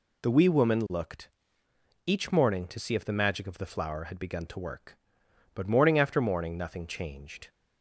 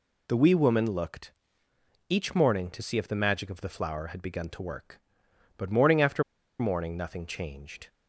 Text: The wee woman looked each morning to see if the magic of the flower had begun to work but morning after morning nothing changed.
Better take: first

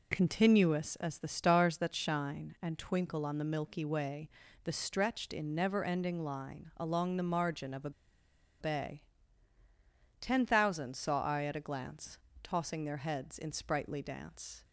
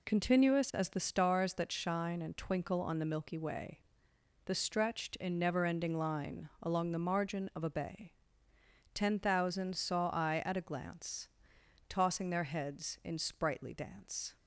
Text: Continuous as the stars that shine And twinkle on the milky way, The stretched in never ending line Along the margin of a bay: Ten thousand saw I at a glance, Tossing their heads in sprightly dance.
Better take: second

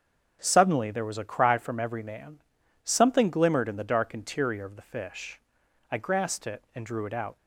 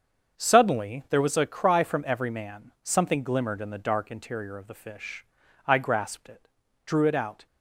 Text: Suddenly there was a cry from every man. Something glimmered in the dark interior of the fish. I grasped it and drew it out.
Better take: first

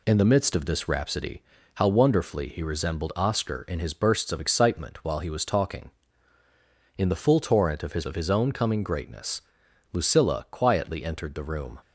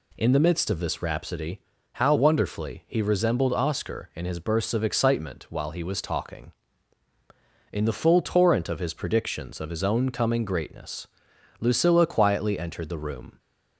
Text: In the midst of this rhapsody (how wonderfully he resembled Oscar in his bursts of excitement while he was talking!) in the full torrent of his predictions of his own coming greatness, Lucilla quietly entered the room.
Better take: second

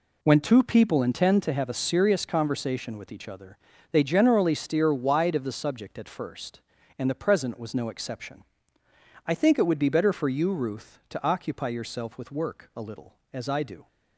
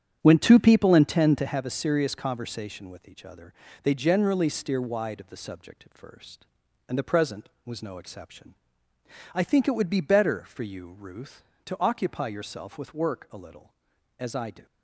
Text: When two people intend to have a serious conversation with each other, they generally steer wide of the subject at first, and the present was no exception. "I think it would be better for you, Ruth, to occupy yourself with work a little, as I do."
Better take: first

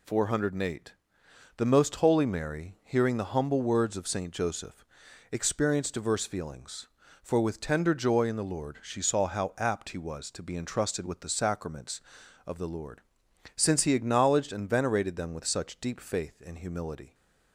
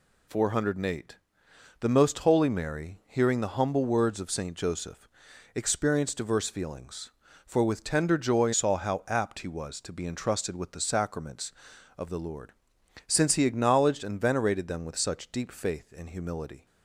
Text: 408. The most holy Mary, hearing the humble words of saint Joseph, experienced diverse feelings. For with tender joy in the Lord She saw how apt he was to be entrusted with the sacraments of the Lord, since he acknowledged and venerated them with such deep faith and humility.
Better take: first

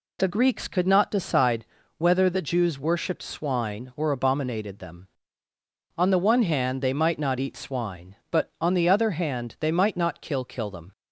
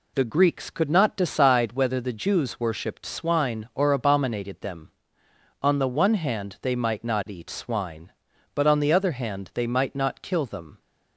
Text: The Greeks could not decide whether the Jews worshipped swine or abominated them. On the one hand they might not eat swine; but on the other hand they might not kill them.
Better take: second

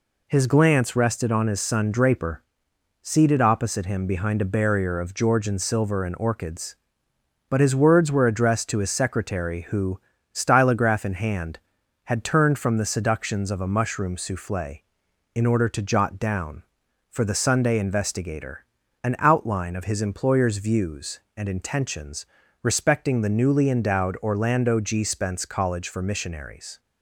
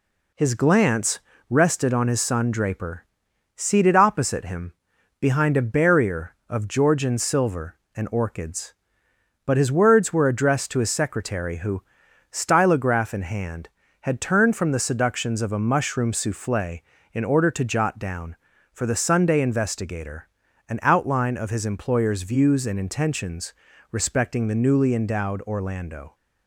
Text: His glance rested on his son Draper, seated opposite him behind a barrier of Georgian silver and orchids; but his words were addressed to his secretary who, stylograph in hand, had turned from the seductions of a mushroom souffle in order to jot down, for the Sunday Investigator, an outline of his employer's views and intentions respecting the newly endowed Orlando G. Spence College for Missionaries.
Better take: first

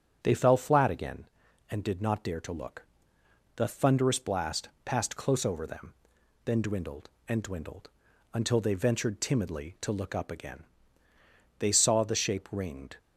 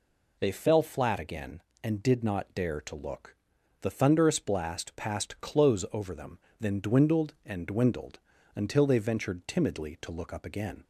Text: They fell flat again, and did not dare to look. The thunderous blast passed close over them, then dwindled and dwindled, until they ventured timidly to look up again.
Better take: second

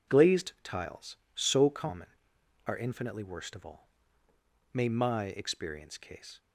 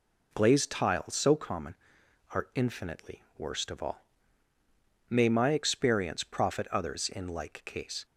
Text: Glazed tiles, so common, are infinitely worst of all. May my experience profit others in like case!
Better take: second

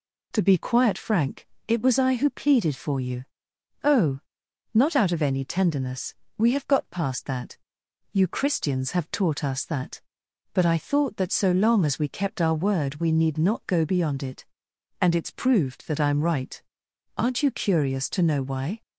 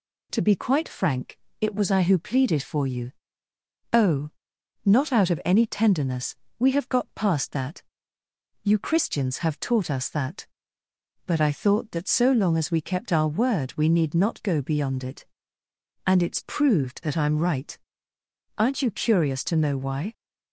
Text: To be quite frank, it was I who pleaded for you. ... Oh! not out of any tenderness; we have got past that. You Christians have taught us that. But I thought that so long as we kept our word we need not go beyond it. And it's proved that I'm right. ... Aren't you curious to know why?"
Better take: second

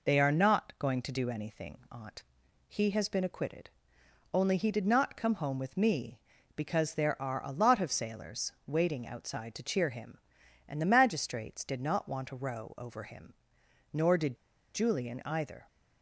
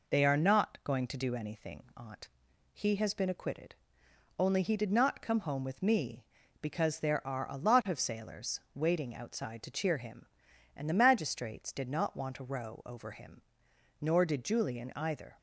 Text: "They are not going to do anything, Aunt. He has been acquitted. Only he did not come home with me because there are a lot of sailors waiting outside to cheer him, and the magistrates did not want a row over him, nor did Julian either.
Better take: second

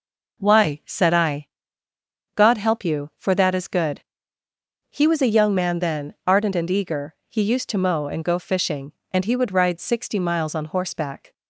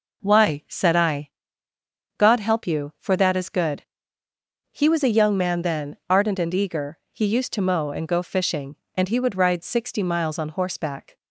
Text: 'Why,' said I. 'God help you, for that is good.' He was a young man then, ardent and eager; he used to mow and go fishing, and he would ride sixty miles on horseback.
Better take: neither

